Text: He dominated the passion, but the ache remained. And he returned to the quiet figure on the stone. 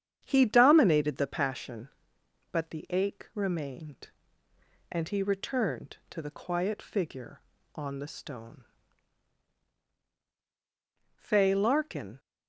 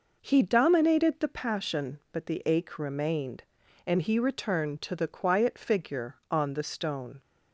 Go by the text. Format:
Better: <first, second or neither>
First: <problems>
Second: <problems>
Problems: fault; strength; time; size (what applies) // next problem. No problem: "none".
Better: second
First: starts louder than the rest; strong; until 1.2 s; 9 dB // goes on to say "Fay Larkin"; noticeable; from 11.1 s on; 1.0 s long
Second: none